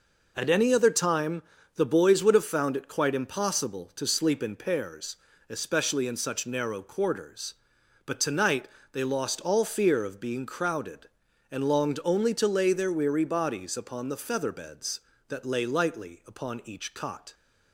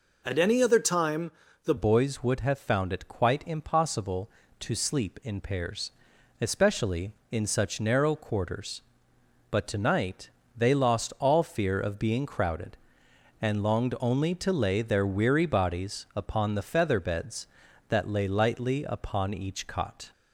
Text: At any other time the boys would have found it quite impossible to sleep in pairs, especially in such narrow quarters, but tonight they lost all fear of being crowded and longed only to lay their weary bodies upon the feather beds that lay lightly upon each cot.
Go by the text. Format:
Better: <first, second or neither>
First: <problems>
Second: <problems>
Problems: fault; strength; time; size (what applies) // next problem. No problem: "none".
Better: first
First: pauses between "time" and "the"; slight; at 1.4 s; 0.34 s long // pauses between "tonight" and "they"; slight; at 8.6 s; 0.24 s long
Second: pauses between "time" and "the"; slight; at 1.3 s; 0.34 s long // changes voice at "boys"; from 1.7 s on; 18.4 s long // pauses between "tonight" and "they"; slight; at 10.3 s; 0.26 s long